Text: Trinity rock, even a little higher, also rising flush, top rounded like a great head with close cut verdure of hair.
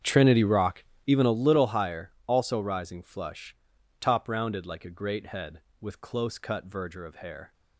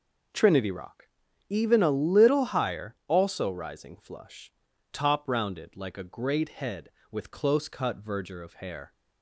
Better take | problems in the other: second | starts louder than the rest; strong; until 1.4 s; 8 dB

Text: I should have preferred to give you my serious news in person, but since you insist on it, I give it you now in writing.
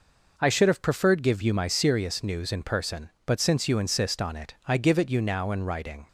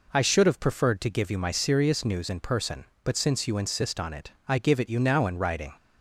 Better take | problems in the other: second | skips "to"; at 1.2 s

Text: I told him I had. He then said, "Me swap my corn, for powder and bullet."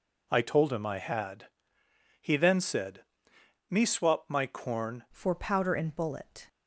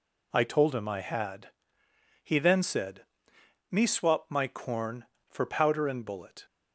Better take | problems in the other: second | changes voice at "for"; from 5.1 s on; 1.3 s long

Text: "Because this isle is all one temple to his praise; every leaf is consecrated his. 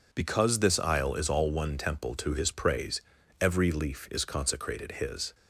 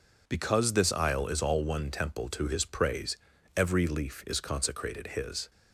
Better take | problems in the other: neither | none

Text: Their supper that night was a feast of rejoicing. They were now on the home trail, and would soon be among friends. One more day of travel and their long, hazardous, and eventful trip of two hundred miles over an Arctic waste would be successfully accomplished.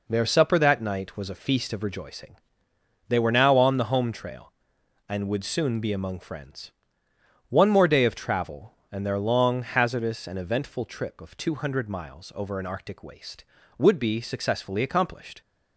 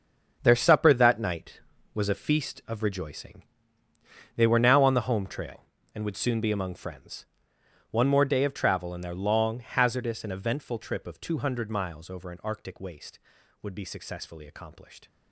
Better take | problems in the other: first | gets quieter; strong; throughout; 11.5 dB

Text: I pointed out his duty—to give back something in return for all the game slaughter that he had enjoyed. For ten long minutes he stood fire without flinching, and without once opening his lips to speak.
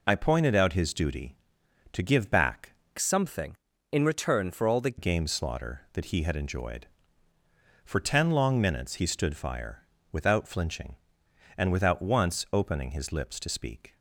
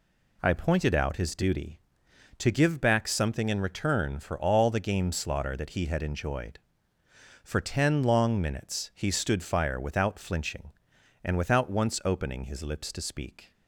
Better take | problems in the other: second | changes voice from "something" to "the"; from 2.9 to 4.9 s; 2.0 s long // pauses between "fire" and "without"; slight; at 9.8 s; 0.30 s long

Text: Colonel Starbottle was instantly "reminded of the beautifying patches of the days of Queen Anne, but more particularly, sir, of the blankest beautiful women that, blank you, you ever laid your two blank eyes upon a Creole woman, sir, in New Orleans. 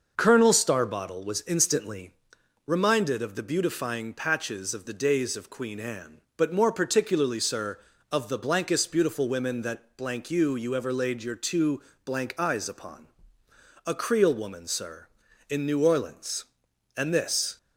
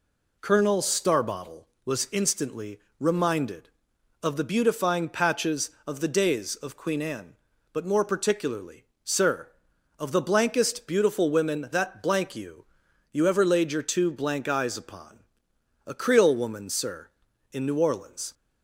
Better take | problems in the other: second | starts louder than the rest; noticeable; until 1.1 s; 6 dB // pauses between "instantly" and "reminded"; noticeable; at 2.1 s; 0.54 s long; slight in the second // pauses between "two" and "blank"; slight; at 11.8 s; 0.24 s long // pauses between "upon" and "a"; noticeable; at 13.0 s; 0.80 s long; noticeable in the second // goes on to say "And this"; noticeable; from 16.9 s on; 0.62 s long

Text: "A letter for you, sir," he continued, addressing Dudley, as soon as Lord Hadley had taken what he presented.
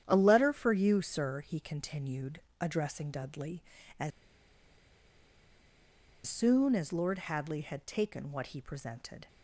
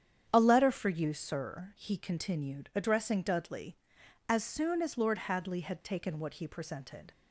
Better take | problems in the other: second | starts louder than the rest; strong; until 1.0 s; 10 dB; strong in the second // pauses between "as" and "soon"; strong; at 4.1 s; 2.1 s long

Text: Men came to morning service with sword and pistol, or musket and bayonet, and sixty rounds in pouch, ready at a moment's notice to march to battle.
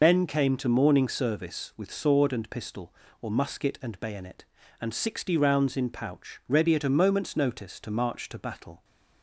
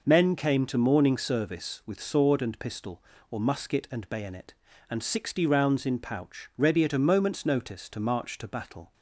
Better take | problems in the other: second | loses the start of "Men"; at 0.0 s; 60 ms

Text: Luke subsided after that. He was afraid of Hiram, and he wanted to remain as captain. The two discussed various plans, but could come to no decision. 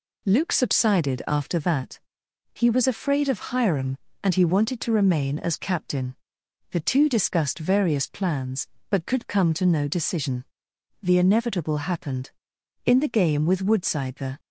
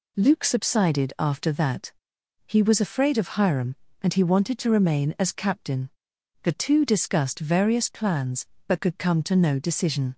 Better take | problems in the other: second | goes on to say "The inevitable happened In the game with Woodside the"; strong; from 11.0 s on; 3.3 s long

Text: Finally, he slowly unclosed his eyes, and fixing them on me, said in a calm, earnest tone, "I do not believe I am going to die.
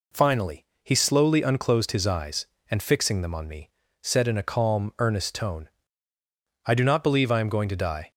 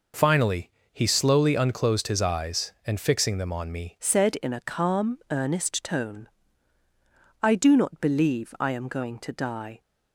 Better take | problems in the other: first | changes voice at "said"; from 3.9 s on; 5.9 s long

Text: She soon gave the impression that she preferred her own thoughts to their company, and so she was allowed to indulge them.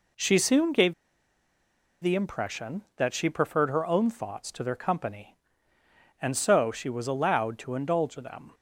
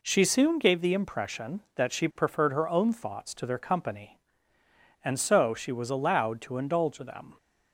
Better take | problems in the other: second | pauses between "gave" and "the"; at 0.9 s; 1.0 s long

